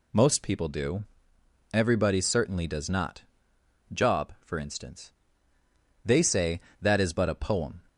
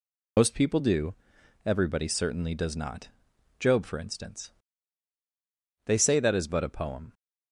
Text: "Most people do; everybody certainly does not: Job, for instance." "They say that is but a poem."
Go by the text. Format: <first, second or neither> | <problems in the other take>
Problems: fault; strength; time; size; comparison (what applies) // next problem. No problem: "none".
first | loses the start of "Most"; at 0.3 s; 85 ms